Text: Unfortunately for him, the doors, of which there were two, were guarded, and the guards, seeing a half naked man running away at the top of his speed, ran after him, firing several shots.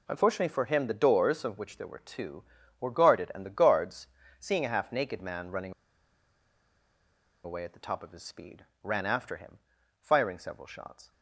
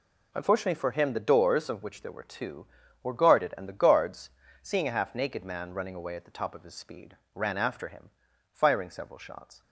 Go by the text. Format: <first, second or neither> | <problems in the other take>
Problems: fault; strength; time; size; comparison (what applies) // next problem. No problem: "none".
second | pauses between "running" and "away"; strong; at 5.7 s; 1.7 s long